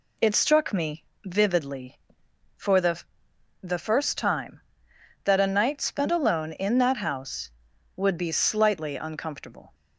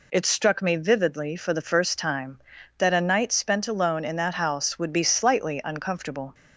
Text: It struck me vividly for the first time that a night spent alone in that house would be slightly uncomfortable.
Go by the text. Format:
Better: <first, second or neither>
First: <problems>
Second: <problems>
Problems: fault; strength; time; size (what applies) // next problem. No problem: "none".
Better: second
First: pauses between "me" and "vividly"; slight; at 1.0 s; 0.20 s long // says "the" twice; at 3.6 s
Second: none